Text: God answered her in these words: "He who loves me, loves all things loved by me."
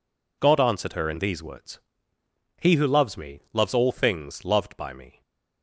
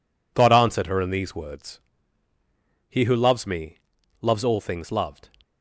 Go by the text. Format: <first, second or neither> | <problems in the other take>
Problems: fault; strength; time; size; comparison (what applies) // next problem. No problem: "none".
first | stops before "by me"; at 5.4 s